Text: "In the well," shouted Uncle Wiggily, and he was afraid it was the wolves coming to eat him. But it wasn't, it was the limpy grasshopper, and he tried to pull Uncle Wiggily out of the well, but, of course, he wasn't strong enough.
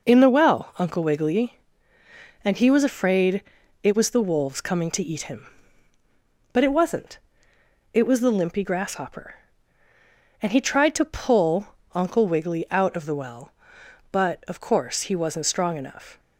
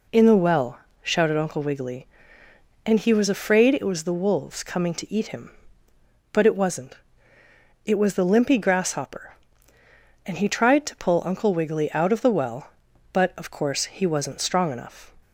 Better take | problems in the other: second | skips "shouted"; at 0.7 s // pauses between "afraid" and "it"; at 3.4 s; 0.42 s long // pauses between "pull" and "Uncle"; slight; at 11.6 s; 0.26 s long

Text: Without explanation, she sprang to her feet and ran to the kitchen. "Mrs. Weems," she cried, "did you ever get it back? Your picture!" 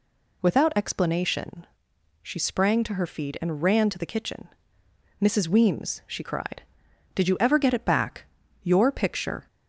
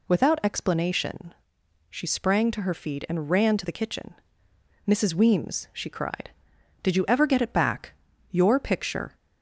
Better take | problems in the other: neither | none

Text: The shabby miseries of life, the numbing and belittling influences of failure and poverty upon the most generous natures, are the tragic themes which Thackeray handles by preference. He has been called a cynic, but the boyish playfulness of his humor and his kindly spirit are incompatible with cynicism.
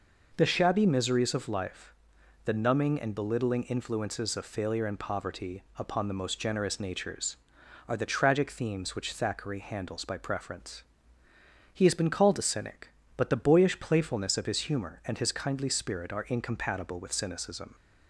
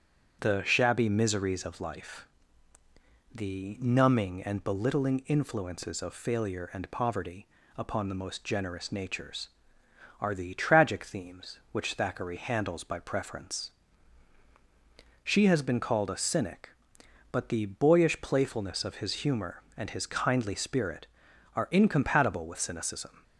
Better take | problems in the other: first | starts louder than the rest; strong; until 1.4 s; 7.5 dB // pauses between "poverty" and "upon"; slight; at 7.4 s; 0.30 s long; slight in the first // says "She" for "He"; at 15.2 s

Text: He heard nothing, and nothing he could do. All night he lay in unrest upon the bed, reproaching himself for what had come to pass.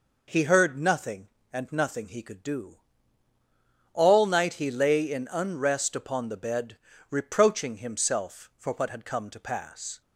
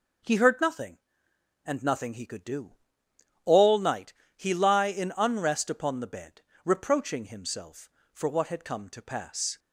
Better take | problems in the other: first | pauses between "night" and "he"; slight; at 4.1 s; 0.24 s long // says "lie" for "lay"; at 4.5 s

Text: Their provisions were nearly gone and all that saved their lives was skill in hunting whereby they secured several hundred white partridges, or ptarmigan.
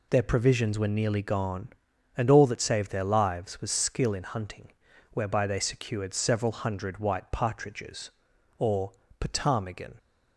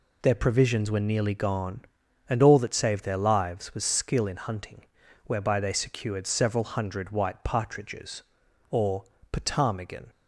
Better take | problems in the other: neither | pauses between "hunting" and "whereby"; the same in both // pauses between "or" and "ptarmigan"; slight; the same in both

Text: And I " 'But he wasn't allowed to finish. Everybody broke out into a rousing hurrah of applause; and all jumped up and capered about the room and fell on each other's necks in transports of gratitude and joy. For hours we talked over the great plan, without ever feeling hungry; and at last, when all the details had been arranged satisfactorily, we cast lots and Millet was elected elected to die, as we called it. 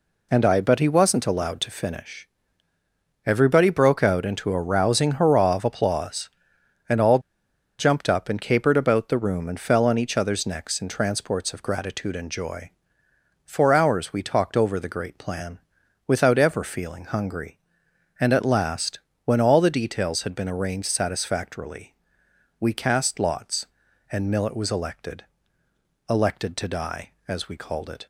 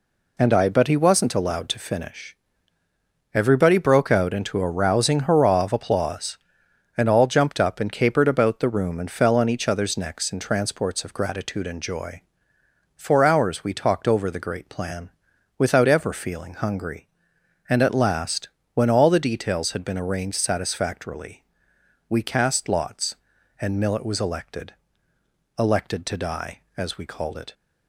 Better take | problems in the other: second | pauses between "all" and "jumped"; noticeable; at 7.1 s; 0.60 s long // pauses between "elected" and "elected"; noticeable; at 25.2 s; 0.84 s long; noticeable in the second

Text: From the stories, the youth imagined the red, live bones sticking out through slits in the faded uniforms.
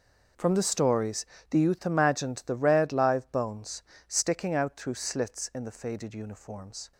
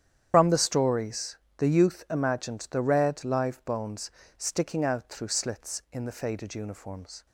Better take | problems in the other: first | loses the start of "From"; at 0.3 s; 80 ms // starts louder than the rest; strong; until 1.3 s; 9.5 dB // pauses between "bones" and "sticking"; slight; at 4.0 s; 0.28 s long; slight in the first

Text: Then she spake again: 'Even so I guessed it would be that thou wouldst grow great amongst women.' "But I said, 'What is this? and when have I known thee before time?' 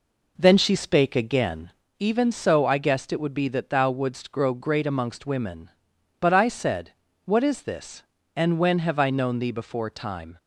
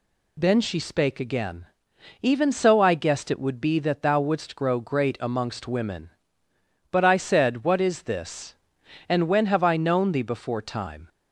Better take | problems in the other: second | starts louder than the rest; noticeable; until 1.9 s; 4 dB

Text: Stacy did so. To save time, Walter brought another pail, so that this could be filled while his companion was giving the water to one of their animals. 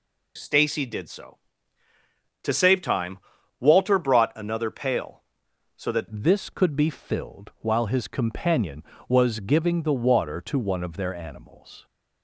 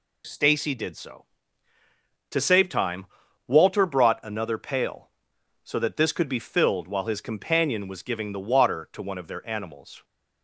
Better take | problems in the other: second | changes voice at "this"; from 6.1 s on; 5.7 s long

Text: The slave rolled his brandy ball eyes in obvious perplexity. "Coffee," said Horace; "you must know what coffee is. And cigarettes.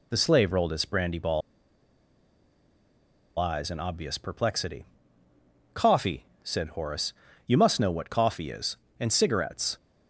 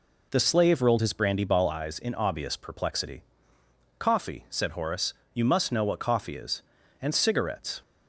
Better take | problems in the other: second | pauses between "ball" and "eyes"; strong; at 1.4 s; 1.9 s long

